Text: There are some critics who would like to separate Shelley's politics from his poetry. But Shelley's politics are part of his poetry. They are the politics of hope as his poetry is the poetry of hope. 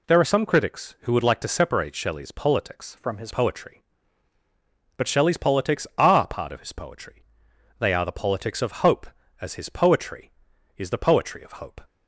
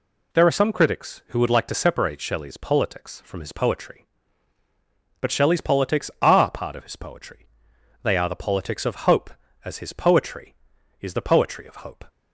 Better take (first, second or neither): second